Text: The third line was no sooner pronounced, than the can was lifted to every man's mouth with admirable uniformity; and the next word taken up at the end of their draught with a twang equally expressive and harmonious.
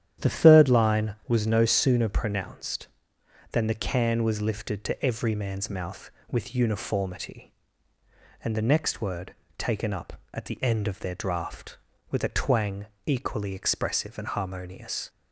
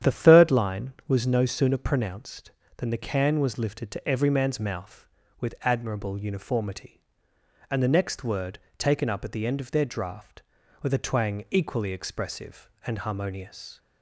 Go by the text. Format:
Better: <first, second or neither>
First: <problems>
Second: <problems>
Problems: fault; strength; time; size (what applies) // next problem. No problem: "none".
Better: second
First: starts louder than the rest; strong; until 1.3 s; 10.5 dB // skips "admirable"; at 6.5 s // pauses between "word" and "taken"; slight; at 9.3 s; 0.24 s long // pauses between "twang" and "equally"; slight; at 12.8 s; 0.18 s long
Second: starts louder than the rest; strong; until 1.1 s; 9.5 dB // pauses between "word" and "taken"; slight; at 8.5 s; 0.20 s long